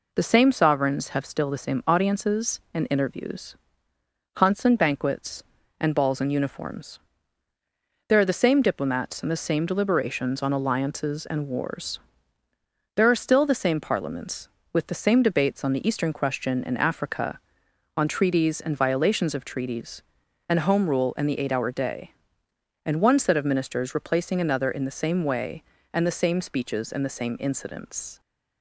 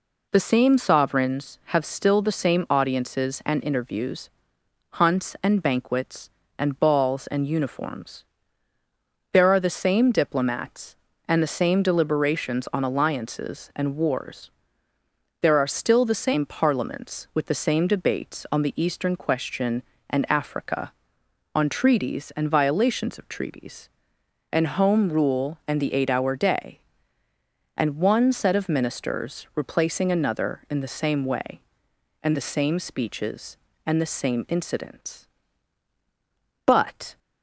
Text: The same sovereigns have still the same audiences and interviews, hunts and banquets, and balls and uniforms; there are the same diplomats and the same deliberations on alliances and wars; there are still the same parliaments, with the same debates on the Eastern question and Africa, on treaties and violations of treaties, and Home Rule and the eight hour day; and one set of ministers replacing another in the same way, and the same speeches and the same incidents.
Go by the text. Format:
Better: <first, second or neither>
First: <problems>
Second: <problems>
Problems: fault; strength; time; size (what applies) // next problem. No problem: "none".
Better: first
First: none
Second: goes on to say "But"; from 36.6 s on; 0.52 s long